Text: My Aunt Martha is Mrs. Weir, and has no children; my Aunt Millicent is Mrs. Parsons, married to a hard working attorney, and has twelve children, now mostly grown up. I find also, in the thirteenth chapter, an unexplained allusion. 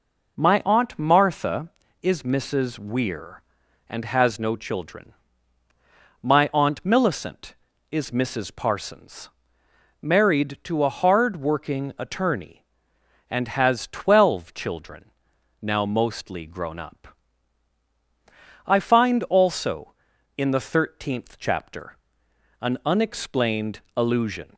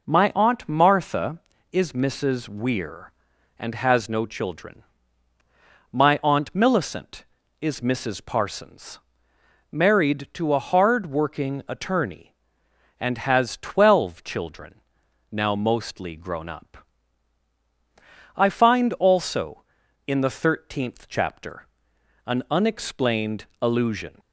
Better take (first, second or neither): neither